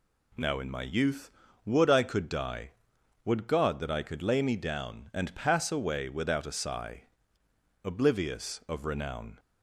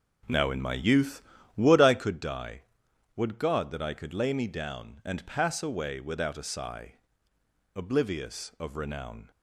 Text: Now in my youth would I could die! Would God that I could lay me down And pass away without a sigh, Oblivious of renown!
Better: first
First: none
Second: starts louder than the rest; noticeable; until 2.2 s; 5 dB

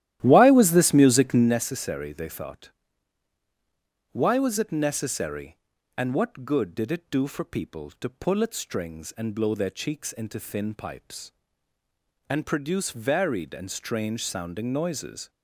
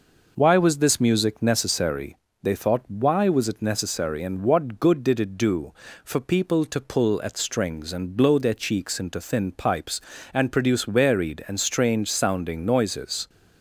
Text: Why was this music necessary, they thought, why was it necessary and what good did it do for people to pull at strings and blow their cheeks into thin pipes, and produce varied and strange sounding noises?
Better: second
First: starts louder than the rest; strong; until 1.5 s; 13 dB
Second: none

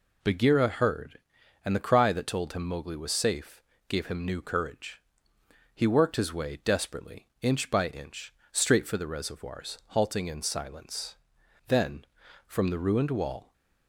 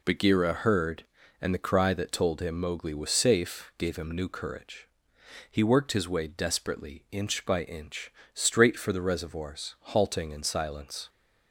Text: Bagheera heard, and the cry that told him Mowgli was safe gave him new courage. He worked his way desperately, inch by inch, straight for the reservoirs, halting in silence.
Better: second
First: pauses between "safe" and "gave"; slight; at 3.6 s; 0.26 s long // goes on to say "Then from the ruined wall"; strong; from 11.6 s on; 1.8 s long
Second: none

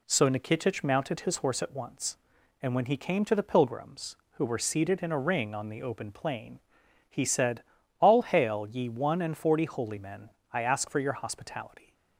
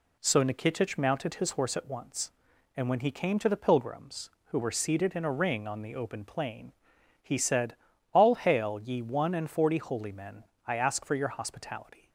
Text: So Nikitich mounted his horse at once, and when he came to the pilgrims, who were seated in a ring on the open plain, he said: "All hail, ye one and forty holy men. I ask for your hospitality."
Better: neither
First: none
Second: none

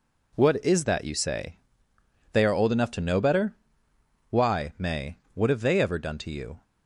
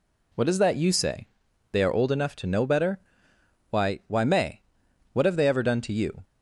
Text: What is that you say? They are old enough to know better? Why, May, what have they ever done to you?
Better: first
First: none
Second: says "Why" twice; at 4.0 s

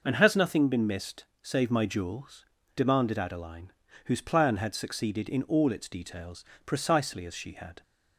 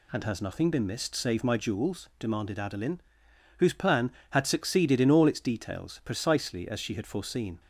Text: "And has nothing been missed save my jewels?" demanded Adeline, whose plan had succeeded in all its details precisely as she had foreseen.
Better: second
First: pauses between "missed" and "save"; slight; at 1.2 s; 0.16 s long // pauses between "details" and "precisely"; slight; at 6.4 s; 0.20 s long // stops before "foreseen"; at 7.8 s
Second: none

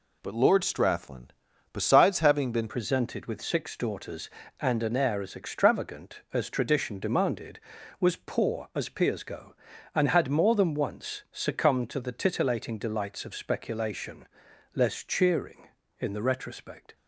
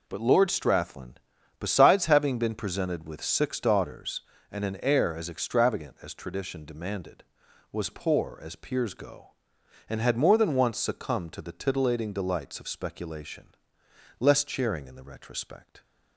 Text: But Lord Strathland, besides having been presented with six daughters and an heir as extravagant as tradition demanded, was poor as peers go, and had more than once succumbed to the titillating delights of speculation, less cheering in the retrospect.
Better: second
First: changes voice at "presented"; from 2.6 s on; 14.3 s long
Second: none

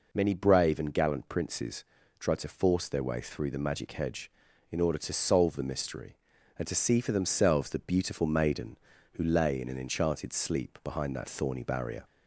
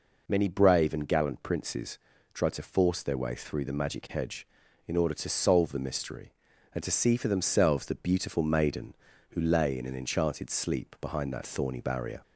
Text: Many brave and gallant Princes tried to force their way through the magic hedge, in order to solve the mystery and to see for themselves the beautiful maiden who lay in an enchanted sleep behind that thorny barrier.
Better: neither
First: pauses between "Princes" and "tried"; slight; at 1.8 s; 0.34 s long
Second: pauses between "Princes" and "tried"; slight; at 1.9 s; 0.34 s long

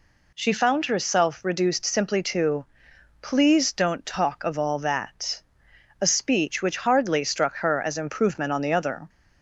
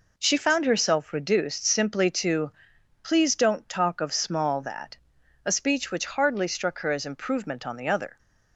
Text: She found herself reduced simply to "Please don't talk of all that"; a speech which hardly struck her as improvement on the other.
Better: first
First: pauses between "to" and "Please"; noticeable; at 2.6 s; 0.56 s long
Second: pauses between "to" and "Please"; noticeable; at 2.4 s; 0.52 s long // says "small" for "all"; at 4.1 s

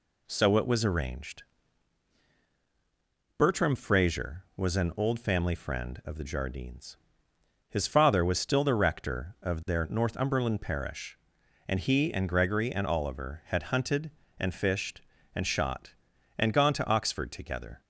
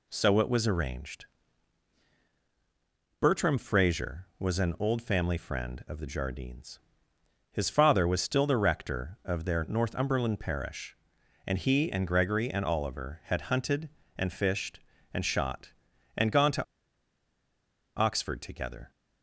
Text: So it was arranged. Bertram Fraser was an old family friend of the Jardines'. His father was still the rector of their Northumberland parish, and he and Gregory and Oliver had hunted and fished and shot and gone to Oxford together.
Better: first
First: none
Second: pauses between "to" and "Oxford"; strong; at 16.6 s; 1.3 s long

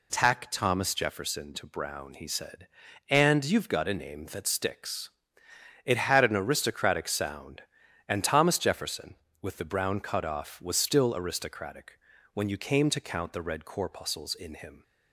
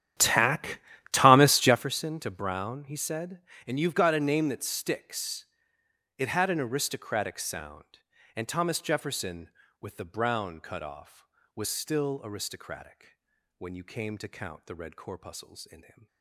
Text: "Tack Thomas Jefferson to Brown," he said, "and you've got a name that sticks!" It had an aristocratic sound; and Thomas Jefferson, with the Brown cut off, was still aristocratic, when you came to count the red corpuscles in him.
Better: first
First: none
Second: starts louder than the rest; strong; until 1.8 s; 11 dB // pauses between "Tack" and "Thomas"; slight; at 0.7 s; 0.32 s long

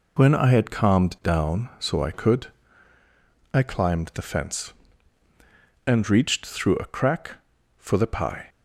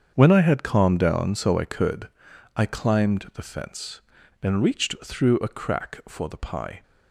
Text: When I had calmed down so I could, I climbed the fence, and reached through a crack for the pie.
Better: first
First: none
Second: gets quieter; strong; throughout; 12 dB

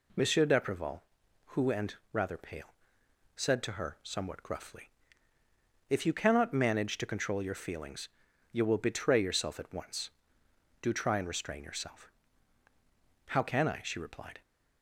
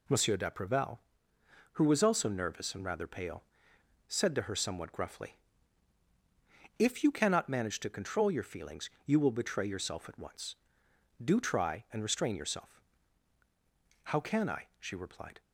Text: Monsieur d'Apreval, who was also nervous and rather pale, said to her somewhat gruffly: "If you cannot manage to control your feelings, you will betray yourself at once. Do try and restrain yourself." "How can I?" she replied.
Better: second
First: skips "was also nervous"; at 1.7 s // pauses between "and" and "rather"; slight; at 1.9 s; 0.16 s long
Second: none

